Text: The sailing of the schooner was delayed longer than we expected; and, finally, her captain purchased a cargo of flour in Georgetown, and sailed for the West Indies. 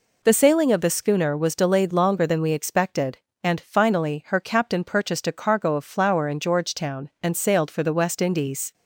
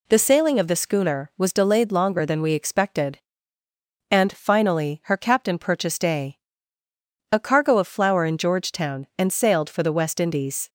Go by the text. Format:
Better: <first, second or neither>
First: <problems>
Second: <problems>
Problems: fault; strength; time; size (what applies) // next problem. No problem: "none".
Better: first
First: none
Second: says "a" twice; at 7.3 s